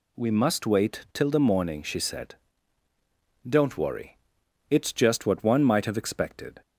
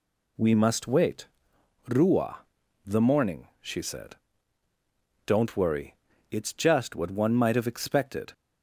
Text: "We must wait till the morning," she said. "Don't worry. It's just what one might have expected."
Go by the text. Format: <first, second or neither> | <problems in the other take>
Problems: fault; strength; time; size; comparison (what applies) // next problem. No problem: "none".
first | says "rua" for "till"; at 1.8 s